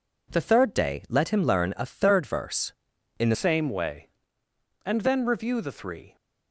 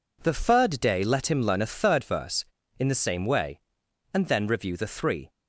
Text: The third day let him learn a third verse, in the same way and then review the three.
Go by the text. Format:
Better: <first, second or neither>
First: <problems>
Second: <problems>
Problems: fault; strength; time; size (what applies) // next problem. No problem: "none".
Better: second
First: changes voice at "same"; from 3.3 s on; 2.8 s long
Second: none